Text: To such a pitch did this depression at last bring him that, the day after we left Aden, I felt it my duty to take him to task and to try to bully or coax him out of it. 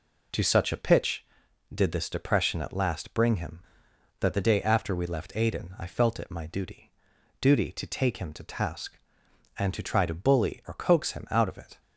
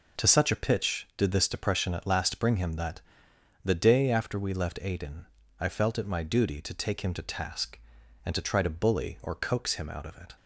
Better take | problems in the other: second | says "duty" twice; at 7.3 s

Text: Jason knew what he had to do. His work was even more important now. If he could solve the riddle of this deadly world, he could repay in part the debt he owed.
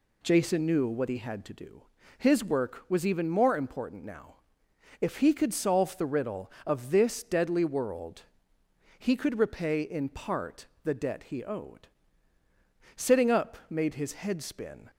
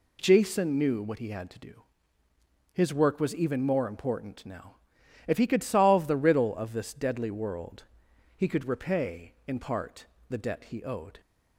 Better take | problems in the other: second | pauses between "part" and "the"; slight; at 10.6 s; 0.18 s long; slight in the second // goes on to say "Sitting up made his head spin"; strong; from 12.9 s on; 1.9 s long

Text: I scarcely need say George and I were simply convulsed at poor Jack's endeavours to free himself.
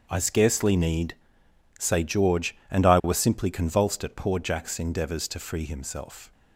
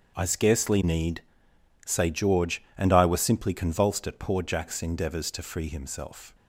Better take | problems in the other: neither | starts louder than the rest; the same in both // pauses between "need" and "say"; noticeable; the same in both

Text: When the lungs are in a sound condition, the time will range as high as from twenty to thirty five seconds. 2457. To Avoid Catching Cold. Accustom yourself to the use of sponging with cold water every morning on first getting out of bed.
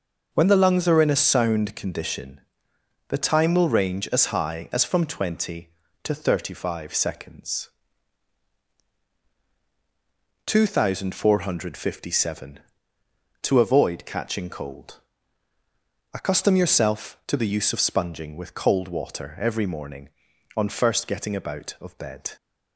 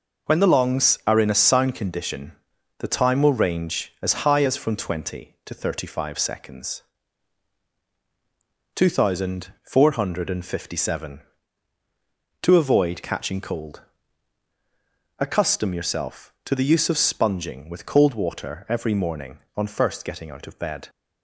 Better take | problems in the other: second | says "about" for "out"; at 21.3 s

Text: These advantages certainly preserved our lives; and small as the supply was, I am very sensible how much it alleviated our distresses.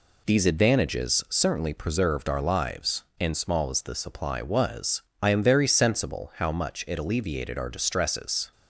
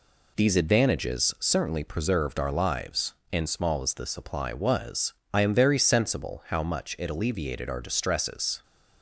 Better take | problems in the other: neither | none

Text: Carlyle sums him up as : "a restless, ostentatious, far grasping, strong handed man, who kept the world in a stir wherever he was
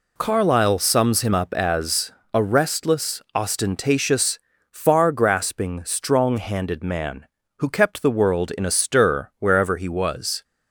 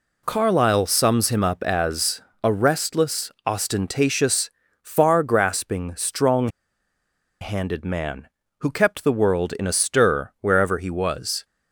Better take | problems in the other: first | pauses between "strong" and "handed"; noticeable; at 6.4 s; 0.92 s long

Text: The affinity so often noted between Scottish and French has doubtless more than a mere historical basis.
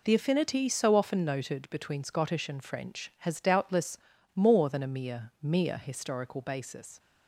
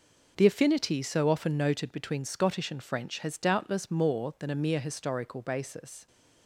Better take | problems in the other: second | pauses between "doubtless" and "more"; at 3.9 s; 0.38 s long // says "mere" twice; at 5.4 s

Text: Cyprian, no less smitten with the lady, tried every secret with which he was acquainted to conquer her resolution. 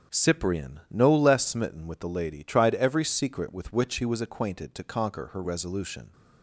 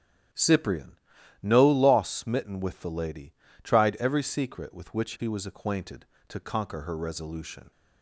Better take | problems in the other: first | starts louder than the rest; strong; until 1.7 s; 10.5 dB; strong in the first // says "loss" for "less"; at 1.6 s

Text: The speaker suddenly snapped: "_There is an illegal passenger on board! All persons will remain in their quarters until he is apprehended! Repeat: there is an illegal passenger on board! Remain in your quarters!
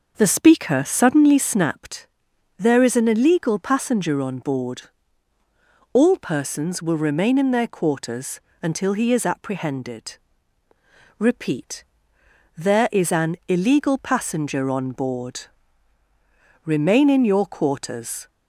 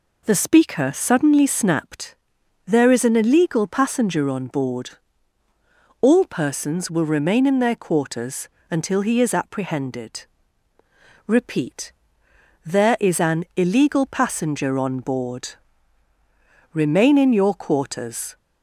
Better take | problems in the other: second | starts louder than the rest; noticeable; until 1.6 s; 6 dB // pauses between "quarters" and "until"; slight; at 8.3 s; 0.24 s long; slight in the second

